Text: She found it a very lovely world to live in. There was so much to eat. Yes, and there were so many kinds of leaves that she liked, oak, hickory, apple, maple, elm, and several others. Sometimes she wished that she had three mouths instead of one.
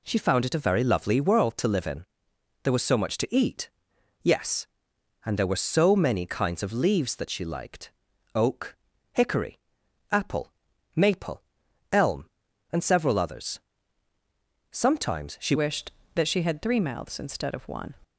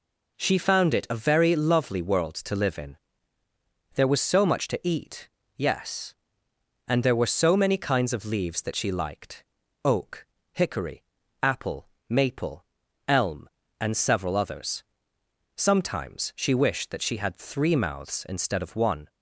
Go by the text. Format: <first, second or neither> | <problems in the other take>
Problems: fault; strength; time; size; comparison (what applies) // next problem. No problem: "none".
second | changes voice at "wished"; from 15.5 s on; 2.4 s long